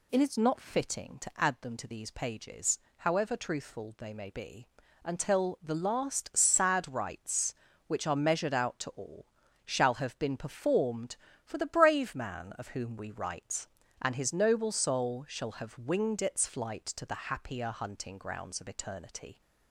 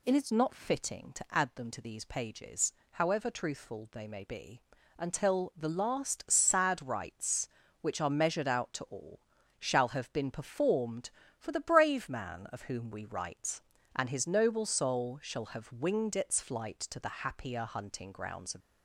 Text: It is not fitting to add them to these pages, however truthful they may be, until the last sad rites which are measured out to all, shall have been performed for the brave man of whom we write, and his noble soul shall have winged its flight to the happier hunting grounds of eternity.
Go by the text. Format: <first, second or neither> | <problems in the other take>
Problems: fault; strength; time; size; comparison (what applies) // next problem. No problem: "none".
first | stops before "eternity"; at 18.6 s